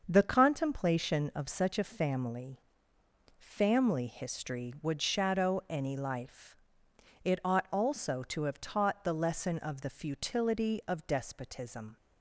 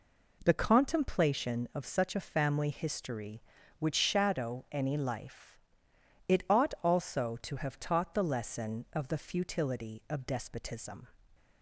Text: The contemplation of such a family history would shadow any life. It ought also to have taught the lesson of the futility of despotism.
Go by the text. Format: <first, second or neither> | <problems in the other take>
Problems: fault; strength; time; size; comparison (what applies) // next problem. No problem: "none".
second | starts louder than the rest; until 1.0 s; 6 dB // says "family" twice; at 3.3 s